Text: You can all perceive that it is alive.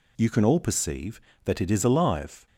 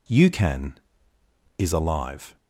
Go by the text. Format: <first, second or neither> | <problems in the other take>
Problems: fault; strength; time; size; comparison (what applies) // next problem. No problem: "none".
first | skips "all perceive that it"; at 1.1 s